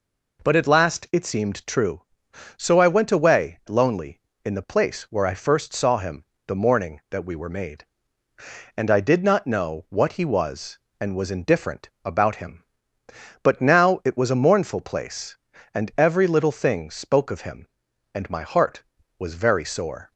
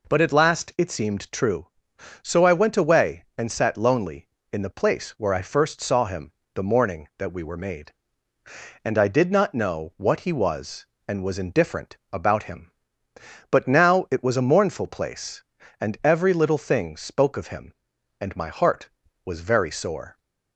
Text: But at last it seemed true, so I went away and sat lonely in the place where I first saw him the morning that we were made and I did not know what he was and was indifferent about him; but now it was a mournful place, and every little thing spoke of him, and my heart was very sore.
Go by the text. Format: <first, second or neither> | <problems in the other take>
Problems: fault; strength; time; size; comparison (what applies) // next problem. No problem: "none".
second | skips "and sat"; at 3.6 s // pauses between "him" and "the"; slight; at 6.2 s; 0.22 s long; slight in the second // pauses between "indifferent" and "about"; slight; at 11.8 s; 0.16 s long; slight in the second